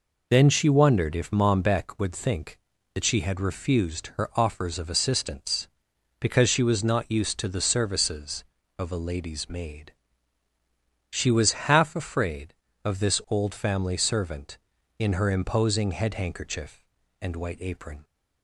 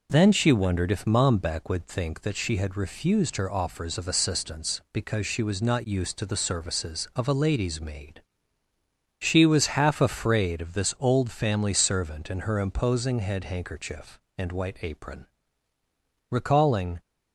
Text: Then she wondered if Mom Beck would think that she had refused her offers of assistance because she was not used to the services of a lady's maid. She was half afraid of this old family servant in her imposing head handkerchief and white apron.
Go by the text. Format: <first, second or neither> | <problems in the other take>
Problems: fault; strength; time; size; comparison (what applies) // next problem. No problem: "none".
first | goes on to say "Recalling"; noticeable; from 16.2 s on; 0.70 s long